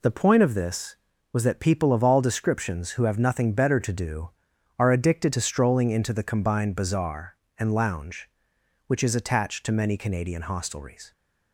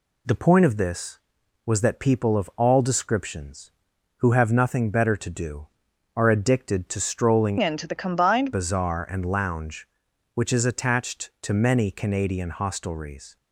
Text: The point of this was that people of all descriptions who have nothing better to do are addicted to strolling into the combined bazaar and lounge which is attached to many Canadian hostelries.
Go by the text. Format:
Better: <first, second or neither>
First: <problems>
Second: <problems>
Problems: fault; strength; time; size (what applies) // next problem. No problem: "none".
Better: first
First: none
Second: changes voice from "into" to "combined"; from 7.6 to 8.5 s; 0.9 s long